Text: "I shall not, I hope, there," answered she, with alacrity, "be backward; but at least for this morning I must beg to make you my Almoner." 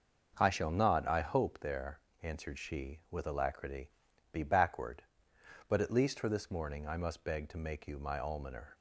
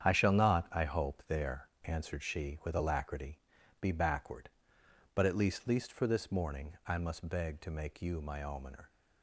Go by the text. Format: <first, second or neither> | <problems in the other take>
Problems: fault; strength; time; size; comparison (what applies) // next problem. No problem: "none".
first | starts louder than the rest; strong; until 1.0 s; 8.5 dB; noticeable in the first // says "least" twice; at 5.6 s